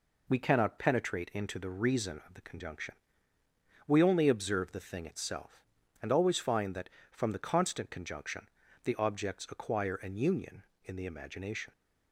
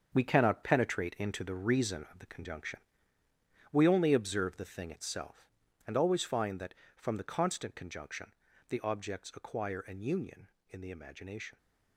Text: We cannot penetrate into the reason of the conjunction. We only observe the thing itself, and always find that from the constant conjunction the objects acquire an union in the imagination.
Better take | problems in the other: first | gets quieter; strong; throughout; 9 dB // pauses between "conjunction" and "the"; slight; at 8.3 s; 0.36 s long; slight in the first

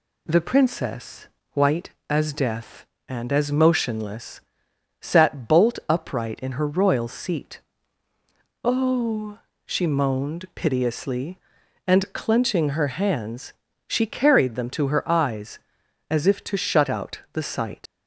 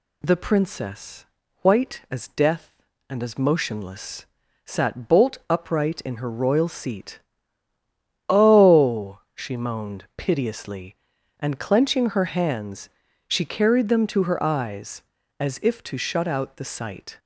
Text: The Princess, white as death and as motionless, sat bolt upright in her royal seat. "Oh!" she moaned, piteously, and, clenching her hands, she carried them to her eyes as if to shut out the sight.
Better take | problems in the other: second | leaves "sight" unfinished; at 17.8 s; 75 ms

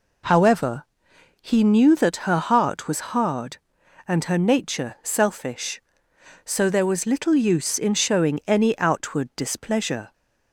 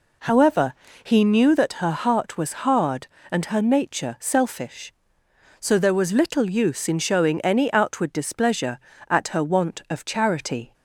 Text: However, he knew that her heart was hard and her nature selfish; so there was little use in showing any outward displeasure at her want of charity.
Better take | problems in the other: second | stops before "at her want of charity"; at 10.1 s

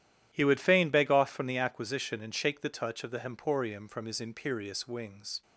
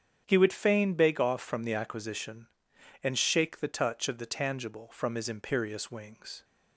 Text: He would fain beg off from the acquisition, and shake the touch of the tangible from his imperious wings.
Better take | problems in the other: second | starts louder than the rest; strong; until 1.3 s; 11.5 dB; strong in the second // says "hemporium" for "tangible"; at 3.1 s

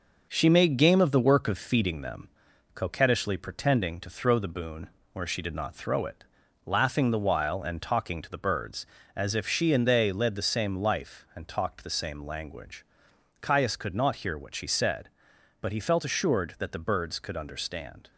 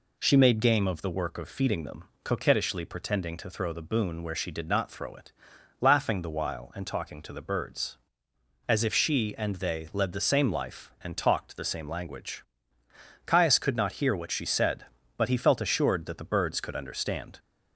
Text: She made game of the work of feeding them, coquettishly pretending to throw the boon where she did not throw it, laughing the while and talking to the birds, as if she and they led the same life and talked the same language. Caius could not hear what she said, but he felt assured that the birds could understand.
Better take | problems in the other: second | gets quieter; noticeable; throughout; 5.5 dB // pauses between "boon" and "where"; slight; at 4.9 s; 0.24 s long

